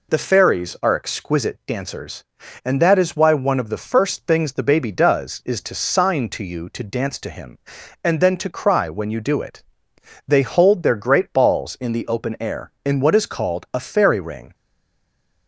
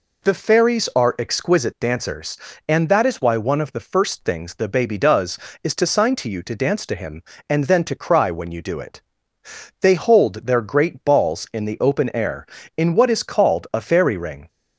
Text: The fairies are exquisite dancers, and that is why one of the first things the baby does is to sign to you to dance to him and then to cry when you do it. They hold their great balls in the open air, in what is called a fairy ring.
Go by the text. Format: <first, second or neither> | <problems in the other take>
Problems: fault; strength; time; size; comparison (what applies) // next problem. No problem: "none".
second | stays silent after the last word; slight; from 14.5 s on; 0.9 s long